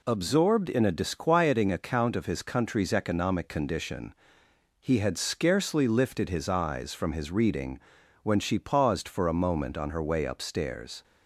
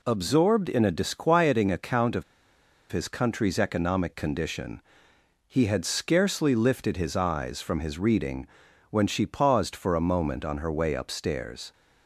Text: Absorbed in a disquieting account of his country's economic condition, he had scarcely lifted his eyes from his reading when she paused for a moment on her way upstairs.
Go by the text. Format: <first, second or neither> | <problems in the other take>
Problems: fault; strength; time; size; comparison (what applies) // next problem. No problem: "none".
first | pauses between "of" and "his"; noticeable; at 2.2 s; 0.68 s long // pauses between "reading" and "when"; at 8.4 s; 0.44 s long; also in the first